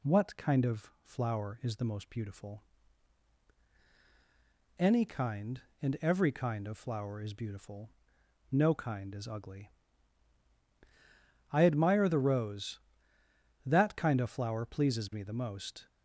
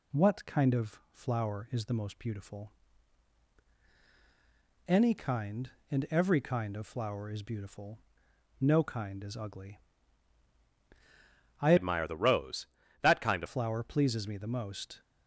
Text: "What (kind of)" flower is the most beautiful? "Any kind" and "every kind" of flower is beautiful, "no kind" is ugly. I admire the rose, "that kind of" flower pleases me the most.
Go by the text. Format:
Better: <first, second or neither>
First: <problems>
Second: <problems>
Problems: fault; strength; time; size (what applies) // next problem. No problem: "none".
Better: first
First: none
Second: changes voice from "admire" to "of"; from 11.7 to 13.4 s; 1.7 s long